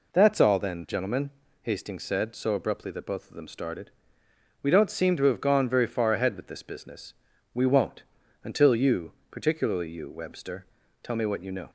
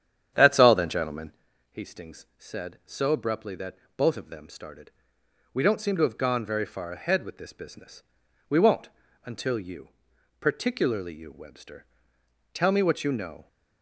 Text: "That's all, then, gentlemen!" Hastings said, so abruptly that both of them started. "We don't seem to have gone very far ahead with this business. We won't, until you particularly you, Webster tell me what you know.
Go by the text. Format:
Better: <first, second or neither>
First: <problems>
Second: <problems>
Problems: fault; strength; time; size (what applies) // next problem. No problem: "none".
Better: first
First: pauses between "you" and "particularly"; slight; at 9.1 s; 0.18 s long // pauses between "Webster" and "tell"; slight; at 10.6 s; 0.36 s long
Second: starts louder than the rest; strong; until 1.5 s; 9 dB // pauses between "that" and "both"; slight; at 3.7 s; 0.22 s long // pauses between "you" and "particularly"; noticeable; at 9.8 s; 0.50 s long // pauses between "Webster" and "tell"; noticeable; at 11.8 s; 0.68 s long